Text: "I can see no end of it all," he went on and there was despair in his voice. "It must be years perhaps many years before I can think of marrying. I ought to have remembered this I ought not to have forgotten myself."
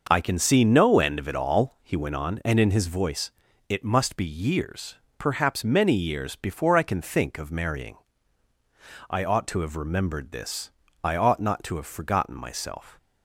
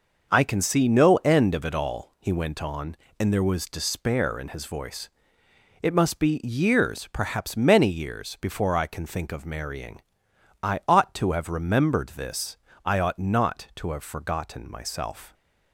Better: second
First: starts louder than the rest; noticeable; until 1.1 s; 6 dB // skips "there was despair"; at 2.5 s // pauses between "years" and "perhaps"; slight; at 4.9 s; 0.22 s long // pauses between "this" and "I"; slight; at 10.6 s; 0.34 s long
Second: pauses between "this" and "I"; slight; at 12.5 s; 0.28 s long

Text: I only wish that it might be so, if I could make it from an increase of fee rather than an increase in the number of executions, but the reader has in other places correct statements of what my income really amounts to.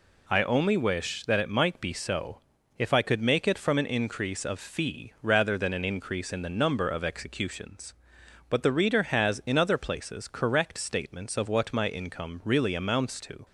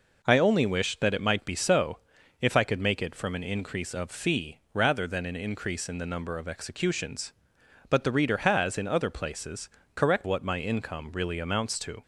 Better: first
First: none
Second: pauses between "places" and "correct"; slight; at 9.6 s; 0.28 s long // skips "statements of"; at 10.2 s

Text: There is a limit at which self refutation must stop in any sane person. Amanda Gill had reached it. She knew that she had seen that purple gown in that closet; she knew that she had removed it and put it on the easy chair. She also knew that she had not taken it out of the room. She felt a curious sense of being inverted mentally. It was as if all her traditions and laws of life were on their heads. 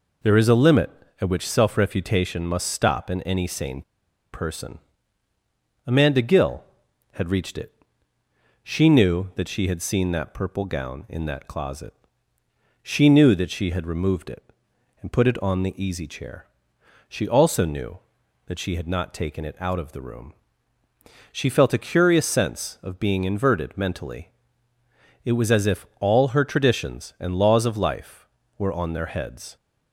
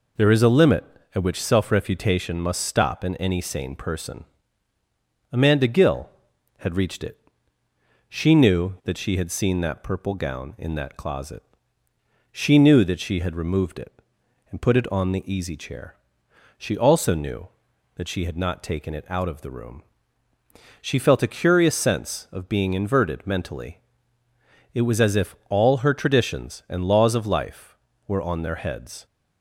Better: second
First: pauses between "sane" and "person"; noticeable; at 3.8 s; 0.50 s long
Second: none

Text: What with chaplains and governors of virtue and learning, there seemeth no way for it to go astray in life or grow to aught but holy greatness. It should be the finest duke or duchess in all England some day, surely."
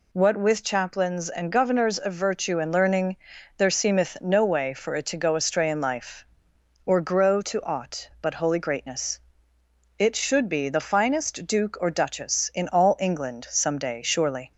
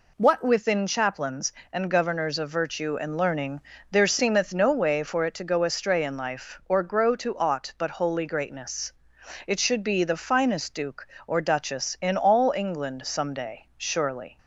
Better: first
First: none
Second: says "within" for "with"; at 0.4 s

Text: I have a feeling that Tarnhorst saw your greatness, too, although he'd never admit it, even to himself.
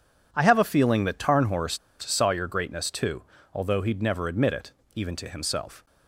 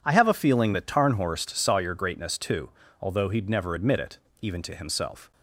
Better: second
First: pauses between "Tarnhorst" and "saw"; slight; at 1.7 s; 0.23 s long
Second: none

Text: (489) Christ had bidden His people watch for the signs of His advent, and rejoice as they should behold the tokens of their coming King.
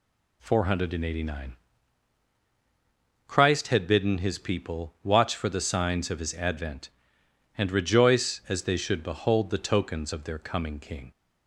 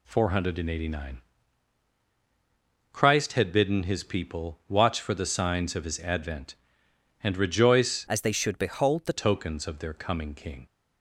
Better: first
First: none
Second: changes voice from "as" to "the"; from 8.0 to 9.1 s; 1.1 s long

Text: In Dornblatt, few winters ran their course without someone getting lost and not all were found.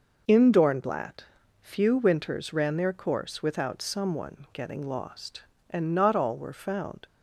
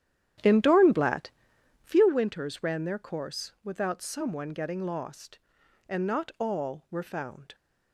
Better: first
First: none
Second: starts louder than the rest; strong; until 2.1 s; 10 dB

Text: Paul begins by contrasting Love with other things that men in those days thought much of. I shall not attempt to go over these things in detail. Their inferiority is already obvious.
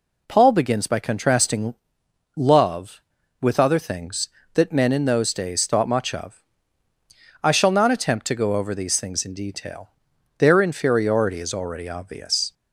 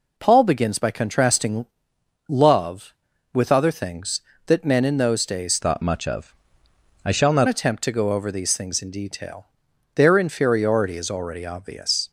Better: first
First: pauses between "contrasting" and "Love"; noticeable; at 1.7 s; 0.59 s long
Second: pauses between "contrasting" and "Love"; noticeable; at 1.6 s; 0.60 s long // changes voice from "thought" to "not"; from 5.6 to 7.4 s; 1.8 s long

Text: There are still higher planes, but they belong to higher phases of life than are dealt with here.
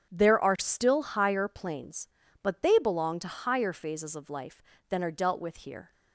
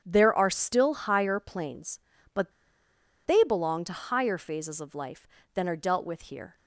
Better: first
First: starts louder than the rest; strong; until 1.1 s; 8 dB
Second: starts louder than the rest; strong; until 1.0 s; 8.5 dB // pauses between "but" and "they"; noticeable; at 2.5 s; 0.75 s long

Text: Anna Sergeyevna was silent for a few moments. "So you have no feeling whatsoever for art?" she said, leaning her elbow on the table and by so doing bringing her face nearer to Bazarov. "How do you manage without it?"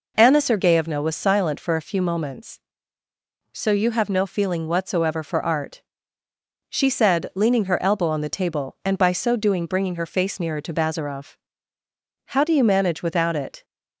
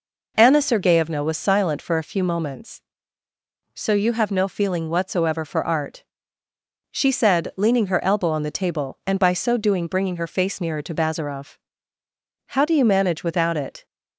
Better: neither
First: none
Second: none

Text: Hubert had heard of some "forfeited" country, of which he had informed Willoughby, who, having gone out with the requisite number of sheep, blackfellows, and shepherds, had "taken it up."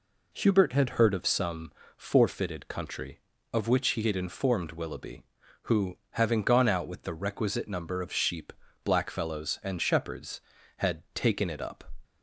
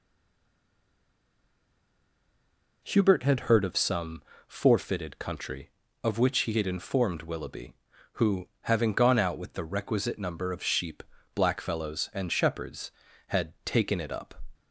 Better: first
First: pauses between "some" and "forfeited"; slight; at 1.7 s; 0.26 s long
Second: stays silent before the first word; strong; until 2.8 s; 2.8 s long // pauses between "some" and "forfeited"; slight; at 4.2 s; 0.26 s long

